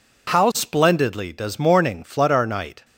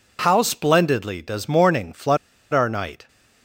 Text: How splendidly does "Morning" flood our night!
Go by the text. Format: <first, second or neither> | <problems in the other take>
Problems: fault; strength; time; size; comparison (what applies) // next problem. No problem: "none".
first | pauses between "flood" and "our"; slight; at 2.1 s; 0.35 s long